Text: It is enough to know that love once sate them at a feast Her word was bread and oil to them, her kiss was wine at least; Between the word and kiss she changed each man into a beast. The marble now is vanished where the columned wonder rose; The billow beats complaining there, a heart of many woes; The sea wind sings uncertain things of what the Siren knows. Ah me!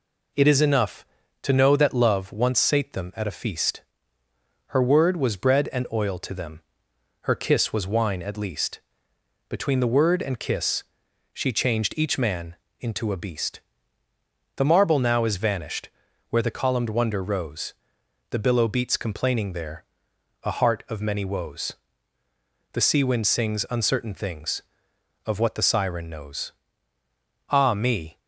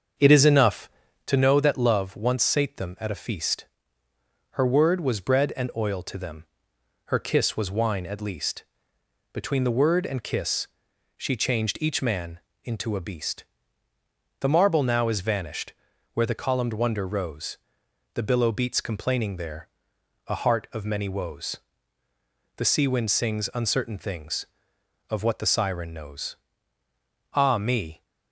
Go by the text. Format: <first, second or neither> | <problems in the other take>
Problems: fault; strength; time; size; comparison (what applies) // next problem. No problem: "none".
first | starts louder than the rest; until 1.4 s; 7 dB // pauses between "feast" and "Her"; noticeable; at 3.6 s; 0.86 s long; noticeable in the first // pauses between "kiss" and "she"; noticeable; at 10.6 s; 0.48 s long; noticeable in the first // pauses between "man" and "into"; slight; at 12.3 s; 0.24 s long; slight in the first // pauses between "vanished" and "where"; at 15.7 s; 0.40 s long; also in the first